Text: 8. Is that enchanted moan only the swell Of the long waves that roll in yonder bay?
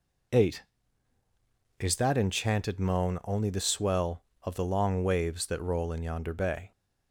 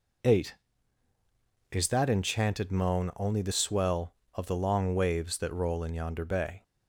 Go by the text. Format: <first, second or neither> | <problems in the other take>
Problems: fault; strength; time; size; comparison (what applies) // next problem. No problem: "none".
neither | none